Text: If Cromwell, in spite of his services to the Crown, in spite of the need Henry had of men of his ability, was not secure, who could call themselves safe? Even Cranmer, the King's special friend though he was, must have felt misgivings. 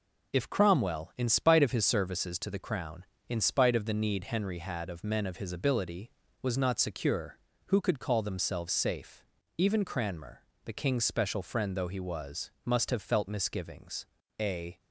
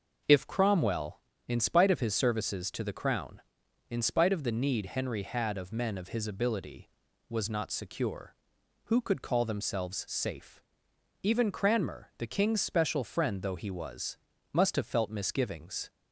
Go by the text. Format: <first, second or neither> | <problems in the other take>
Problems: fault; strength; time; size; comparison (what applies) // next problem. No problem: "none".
second | goes on to say "A"; slight; from 14.3 s on; 0.42 s long